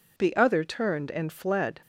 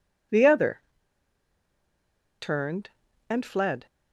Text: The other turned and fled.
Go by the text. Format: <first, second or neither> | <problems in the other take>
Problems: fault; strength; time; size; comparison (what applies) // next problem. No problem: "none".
first | pauses between "other" and "turned"; strong; at 0.8 s; 1.5 s long